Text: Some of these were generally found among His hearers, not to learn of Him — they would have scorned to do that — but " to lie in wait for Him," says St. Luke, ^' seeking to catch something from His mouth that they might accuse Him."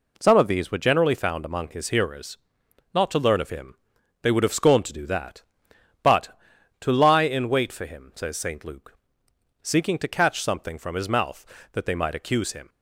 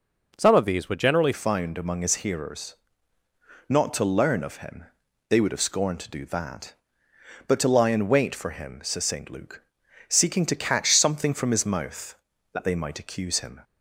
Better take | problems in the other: first | changes voice at "found"; from 1.3 s on; 12.2 s long

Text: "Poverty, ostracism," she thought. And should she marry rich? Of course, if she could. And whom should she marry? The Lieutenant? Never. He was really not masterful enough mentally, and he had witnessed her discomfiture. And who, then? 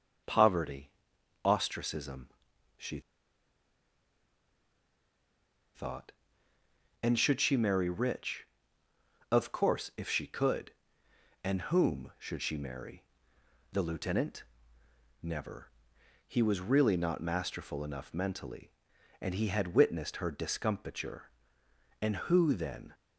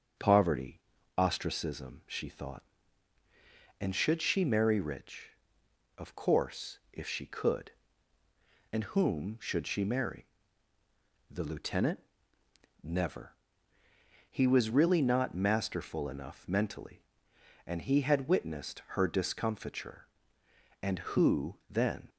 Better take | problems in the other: second | starts louder than the rest; strong; until 1.7 s; 7 dB; strong in the second // pauses between "she" and "thought"; strong; at 2.9 s; 2.7 s long

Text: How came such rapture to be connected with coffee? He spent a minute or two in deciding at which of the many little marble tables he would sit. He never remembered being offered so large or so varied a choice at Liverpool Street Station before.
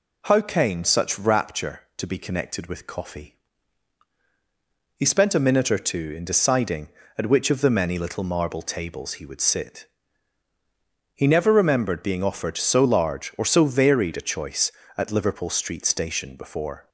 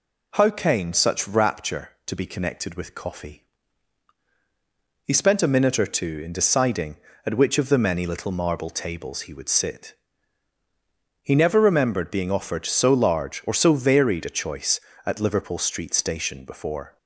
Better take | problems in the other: neither | none

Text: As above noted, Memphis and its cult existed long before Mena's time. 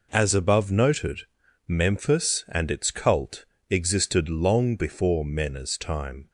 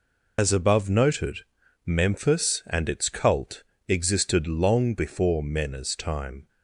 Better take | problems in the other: first | loses the start of "As"; at 0.3 s; 95 ms // pauses between "cult" and "existed"; slight; at 3.6 s; 0.24 s long; slight in the first

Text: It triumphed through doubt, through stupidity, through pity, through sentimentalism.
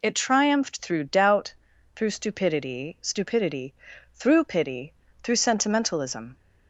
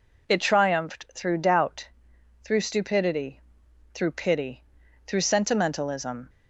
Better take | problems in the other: second | says "stupidity" twice; at 3.0 s

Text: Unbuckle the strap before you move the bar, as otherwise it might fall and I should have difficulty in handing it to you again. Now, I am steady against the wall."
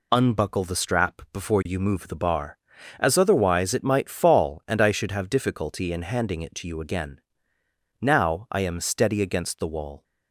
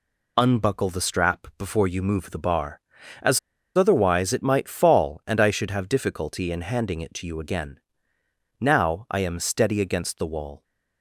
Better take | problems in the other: first | pauses between "as" and "otherwise"; at 3.3 s; 0.37 s long

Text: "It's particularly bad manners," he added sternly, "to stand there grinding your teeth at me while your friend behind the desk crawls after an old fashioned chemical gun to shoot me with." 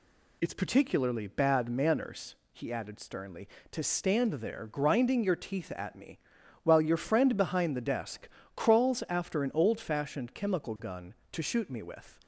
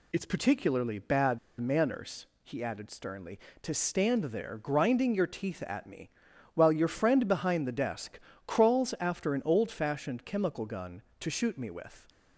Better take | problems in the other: first | pauses between "bad" and "manners"; slight; at 1.3 s; 0.22 s long // pauses between "me" and "while"; at 6.0 s; 0.44 s long; also in the first // pauses between "desk" and "crawls"; slight; at 8.1 s; 0.26 s long; slight in the first

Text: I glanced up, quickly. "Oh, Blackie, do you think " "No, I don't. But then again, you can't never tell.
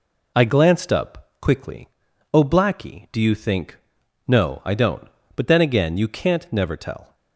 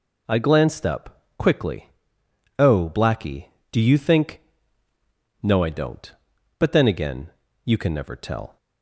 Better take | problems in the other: first | says "can" for "can't"; at 7.7 s

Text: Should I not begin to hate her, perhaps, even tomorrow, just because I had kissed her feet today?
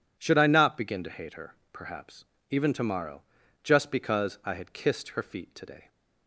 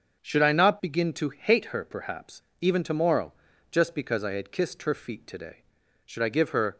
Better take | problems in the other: first | starts louder than the rest; until 1.2 s; 6.5 dB // goes on to say "Should I give her"; noticeable; from 6.0 s on; 0.72 s long

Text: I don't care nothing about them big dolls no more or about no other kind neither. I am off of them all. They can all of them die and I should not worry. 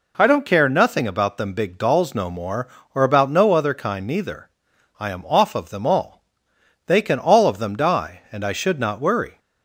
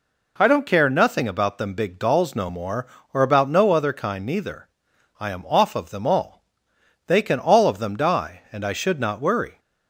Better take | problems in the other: neither | none

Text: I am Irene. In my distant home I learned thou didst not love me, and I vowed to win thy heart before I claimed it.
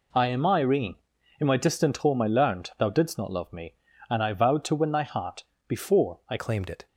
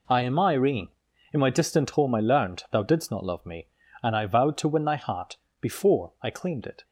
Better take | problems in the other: second | pauses between "heart" and "before"; slight; at 5.4 s; 0.24 s long; slight in the second // changes voice at "claimed"; from 6.3 s on; 0.5 s long

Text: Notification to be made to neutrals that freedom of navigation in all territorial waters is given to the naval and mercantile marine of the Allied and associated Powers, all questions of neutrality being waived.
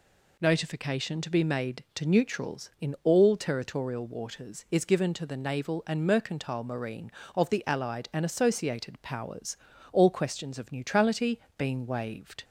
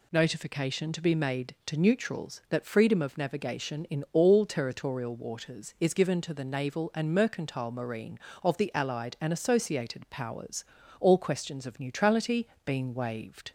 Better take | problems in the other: second | skips "that freedom of navigation"; at 2.7 s // pauses between "neutrality" and "being"; slight; at 11.3 s; 0.16 s long; slight in the second

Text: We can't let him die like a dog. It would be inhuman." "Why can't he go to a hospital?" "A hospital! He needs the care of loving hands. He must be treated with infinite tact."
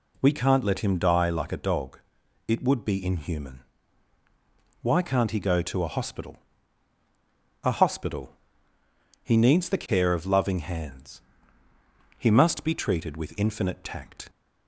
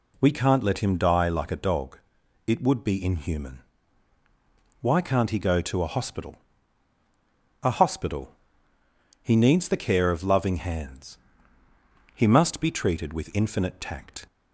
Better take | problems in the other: neither | none

